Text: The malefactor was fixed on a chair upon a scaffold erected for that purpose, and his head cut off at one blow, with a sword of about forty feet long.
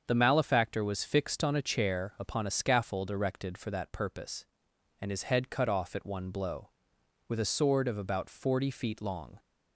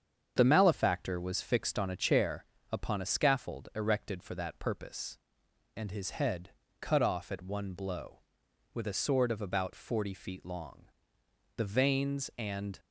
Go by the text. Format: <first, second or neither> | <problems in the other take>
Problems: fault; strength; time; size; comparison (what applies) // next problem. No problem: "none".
first | starts louder than the rest; strong; until 1.3 s; 7.5 dB; also in the first // pauses between "chair" and "upon"; slight; at 2.4 s; 0.26 s long // pauses between "head" and "cut"; slight; at 6.5 s; 0.28 s long // goes on to say "The veins and"; noticeable; from 11.5 s on; 1.2 s long